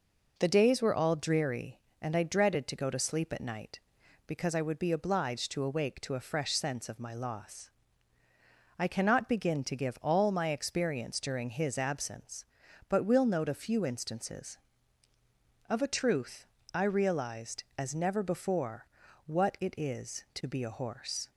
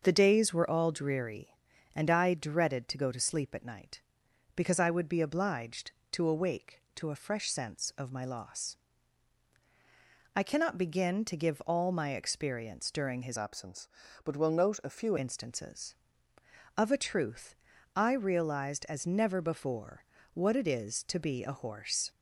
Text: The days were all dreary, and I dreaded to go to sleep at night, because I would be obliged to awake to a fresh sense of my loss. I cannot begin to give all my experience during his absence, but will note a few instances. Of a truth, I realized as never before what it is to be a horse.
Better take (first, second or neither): first